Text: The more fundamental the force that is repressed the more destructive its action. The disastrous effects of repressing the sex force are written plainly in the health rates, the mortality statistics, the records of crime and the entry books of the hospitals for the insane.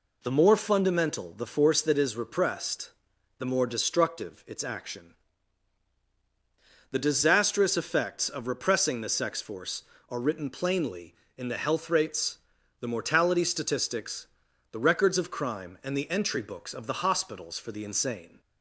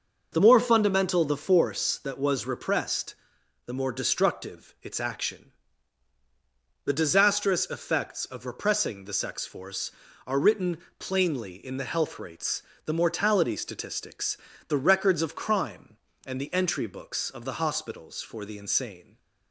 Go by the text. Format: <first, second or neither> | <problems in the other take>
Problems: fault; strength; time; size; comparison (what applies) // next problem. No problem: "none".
first | says "was" for "is"; at 2.1 s // pauses between "repressed" and "the"; noticeable; at 3.1 s; 0.50 s long; noticeable in the first // pauses between "written" and "plainly"; slight; at 10.7 s; 0.20 s long